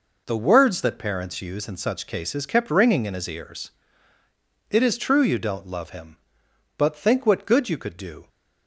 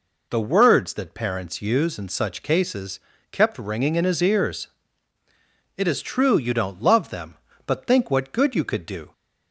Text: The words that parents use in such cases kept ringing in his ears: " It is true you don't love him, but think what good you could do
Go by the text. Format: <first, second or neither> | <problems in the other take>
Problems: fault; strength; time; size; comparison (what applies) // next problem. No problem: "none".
first | pauses between "cases" and "kept"; slight; at 2.9 s; 0.32 s long // says "them" for "him"; at 7.1 s